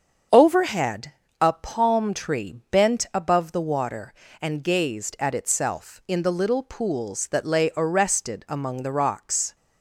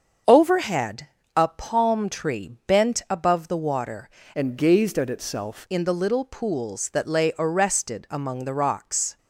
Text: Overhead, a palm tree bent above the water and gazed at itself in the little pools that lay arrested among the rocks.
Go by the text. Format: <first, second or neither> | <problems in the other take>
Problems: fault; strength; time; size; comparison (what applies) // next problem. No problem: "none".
first | starts louder than the rest; until 1.5 s; 7 dB; strong in the first // pauses between "tree" and "bent"; slight; at 2.4 s; 0.18 s long; slight in the first // changes voice from "and" to "itself"; from 4.3 to 5.6 s; 1.3 s long